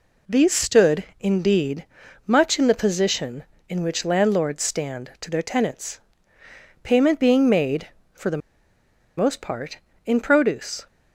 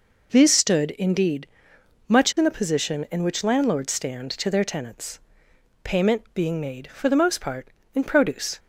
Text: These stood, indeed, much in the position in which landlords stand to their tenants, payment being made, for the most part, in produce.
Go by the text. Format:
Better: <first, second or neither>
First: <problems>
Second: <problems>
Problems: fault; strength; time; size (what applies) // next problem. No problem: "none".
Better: second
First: pauses between "the" and "most"; noticeable; at 8.4 s; 0.79 s long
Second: none